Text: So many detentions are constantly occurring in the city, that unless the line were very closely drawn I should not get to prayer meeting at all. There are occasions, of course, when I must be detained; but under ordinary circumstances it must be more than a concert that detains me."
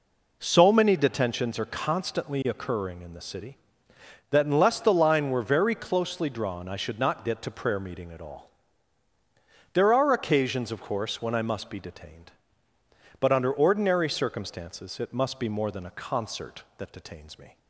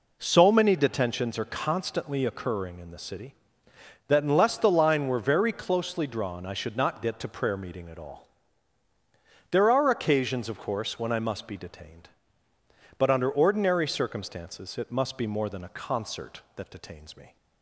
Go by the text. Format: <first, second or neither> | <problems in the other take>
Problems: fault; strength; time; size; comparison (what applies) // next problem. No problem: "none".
neither | none